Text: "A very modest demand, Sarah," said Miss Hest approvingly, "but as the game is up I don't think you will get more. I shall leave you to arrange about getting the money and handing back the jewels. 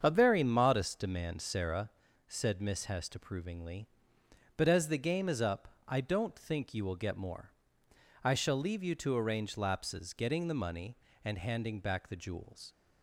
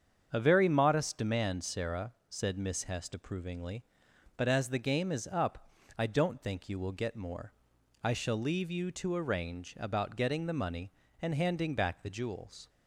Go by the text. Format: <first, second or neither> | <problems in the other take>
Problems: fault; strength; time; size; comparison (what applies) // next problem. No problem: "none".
second | starts louder than the rest; strong; until 1.0 s; 7.5 dB; strong in the second // pauses between "up" and "I"; slight; at 5.6 s; 0.20 s long; slight in the second // says "lapses" for "about"; at 9.5 s